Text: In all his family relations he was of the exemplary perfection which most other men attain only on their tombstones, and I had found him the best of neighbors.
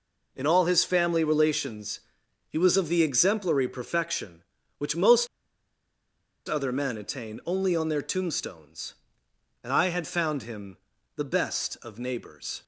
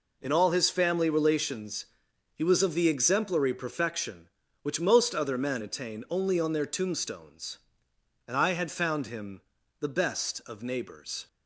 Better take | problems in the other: second | pauses between "relations" and "he"; noticeable; at 2.0 s; 0.48 s long; noticeable in the second // pauses between "most" and "other"; at 5.2 s; 1.2 s long // pauses between "him" and "the"; at 10.7 s; 0.40 s long; also in the second

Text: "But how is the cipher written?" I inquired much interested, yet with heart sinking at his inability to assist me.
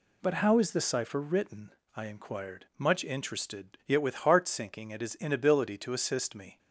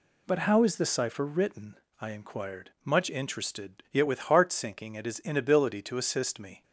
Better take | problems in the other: neither | none

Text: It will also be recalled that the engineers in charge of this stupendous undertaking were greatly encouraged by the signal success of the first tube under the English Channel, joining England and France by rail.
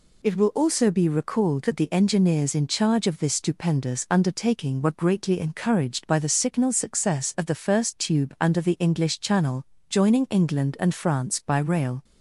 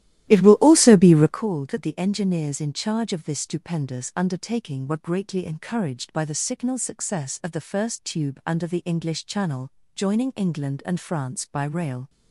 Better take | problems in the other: first | starts louder than the rest; strong; until 1.4 s; 14 dB

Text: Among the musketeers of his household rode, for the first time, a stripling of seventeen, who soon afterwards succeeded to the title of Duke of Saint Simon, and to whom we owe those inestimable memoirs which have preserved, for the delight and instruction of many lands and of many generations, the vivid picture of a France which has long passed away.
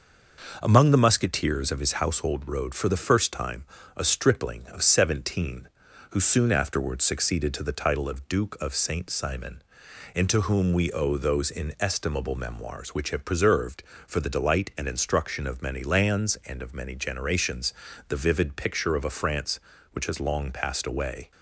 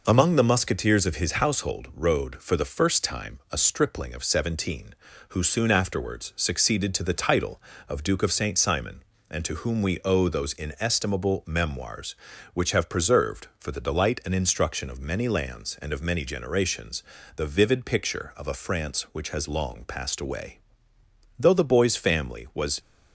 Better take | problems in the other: first | goes on to say "Though the boy's family was"; from 21.3 s on; 1.4 s long

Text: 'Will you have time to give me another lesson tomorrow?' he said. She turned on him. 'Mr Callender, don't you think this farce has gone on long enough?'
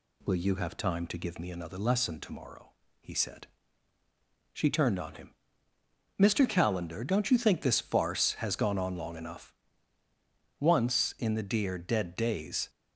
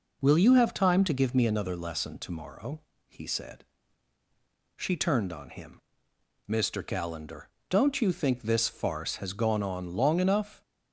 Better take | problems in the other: second | goes on to say "Once in the dear dead days"; strong; from 10.5 s on; 2.1 s long

